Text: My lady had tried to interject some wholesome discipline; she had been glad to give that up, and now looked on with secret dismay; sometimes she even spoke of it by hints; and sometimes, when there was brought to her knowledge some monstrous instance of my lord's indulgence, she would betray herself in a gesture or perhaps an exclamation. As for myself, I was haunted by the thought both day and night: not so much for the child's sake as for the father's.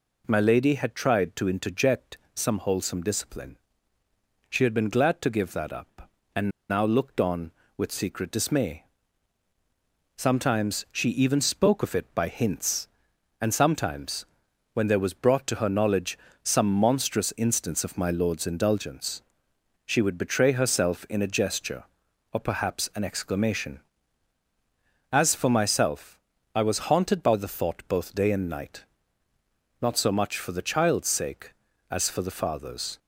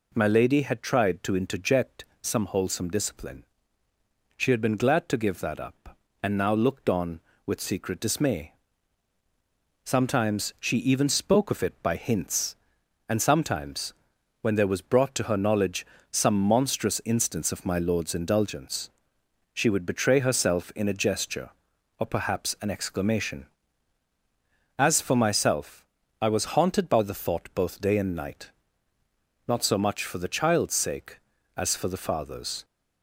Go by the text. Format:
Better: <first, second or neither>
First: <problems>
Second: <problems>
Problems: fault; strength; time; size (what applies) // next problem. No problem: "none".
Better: second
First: pauses between "interject" and "some"; slight; at 2.1 s; 0.16 s long // pauses between "and" and "now"; slight; at 6.4 s; 0.20 s long // pauses between "knowledge" and "some"; slight; at 16.1 s; 0.24 s long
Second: pauses between "interject" and "some"; slight; at 2.0 s; 0.16 s long // pauses between "knowledge" and "some"; slight; at 15.8 s; 0.24 s long